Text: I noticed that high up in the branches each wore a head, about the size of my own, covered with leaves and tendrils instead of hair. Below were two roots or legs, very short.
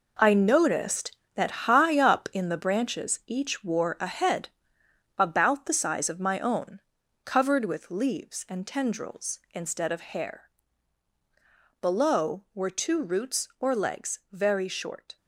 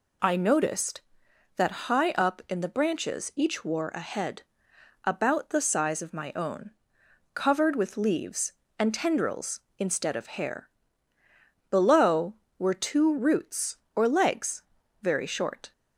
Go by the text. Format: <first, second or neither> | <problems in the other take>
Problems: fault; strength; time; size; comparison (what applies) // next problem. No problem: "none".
second | gets quieter; strong; throughout; 9.5 dB